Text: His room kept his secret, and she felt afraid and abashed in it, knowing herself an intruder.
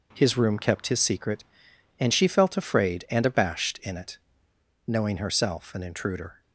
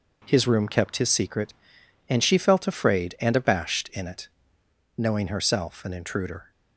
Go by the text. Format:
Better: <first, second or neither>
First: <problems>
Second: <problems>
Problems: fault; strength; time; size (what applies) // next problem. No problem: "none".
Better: neither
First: none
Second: none